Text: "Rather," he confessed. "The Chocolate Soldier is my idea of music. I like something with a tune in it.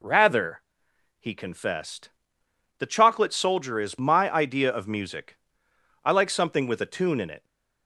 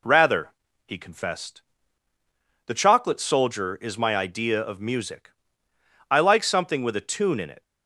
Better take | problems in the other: neither | none

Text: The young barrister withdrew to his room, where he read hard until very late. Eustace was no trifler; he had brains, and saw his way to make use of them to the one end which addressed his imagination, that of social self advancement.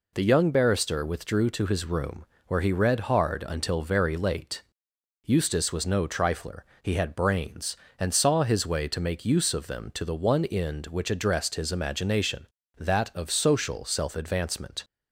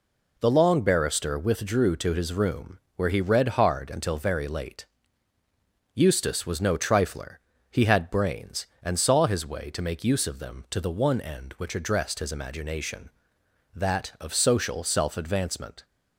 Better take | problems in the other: first | says "long" for "young"; at 0.5 s

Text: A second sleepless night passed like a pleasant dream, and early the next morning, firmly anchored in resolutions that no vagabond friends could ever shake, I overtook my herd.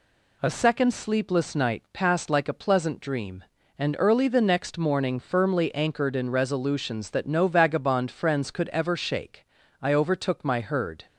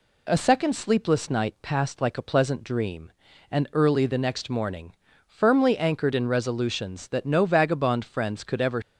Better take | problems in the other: first | stops before "shake I overtook my herd"; at 8.8 s

